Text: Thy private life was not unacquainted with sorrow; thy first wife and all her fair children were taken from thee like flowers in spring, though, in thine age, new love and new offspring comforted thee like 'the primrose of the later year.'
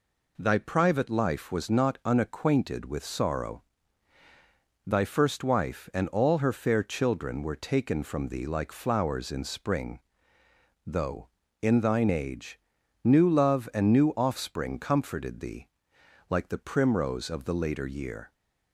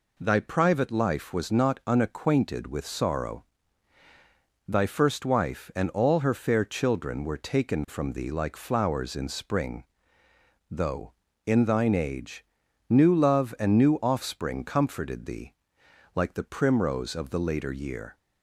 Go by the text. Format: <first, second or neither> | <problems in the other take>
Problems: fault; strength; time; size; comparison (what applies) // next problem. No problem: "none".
neither | pauses between "thee" and "like"; noticeable; the same in both